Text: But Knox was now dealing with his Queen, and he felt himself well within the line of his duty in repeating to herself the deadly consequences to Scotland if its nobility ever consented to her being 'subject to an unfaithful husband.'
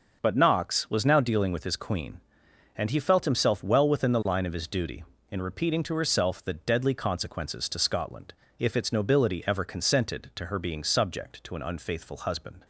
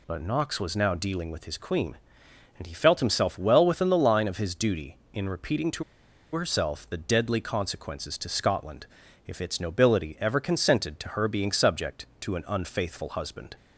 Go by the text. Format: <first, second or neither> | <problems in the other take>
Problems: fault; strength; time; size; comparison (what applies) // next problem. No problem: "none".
first | pauses between "to" and "herself"; noticeable; at 5.8 s; 0.50 s long // pauses between "Scotland" and "if"; at 8.8 s; 0.42 s long; slight in the first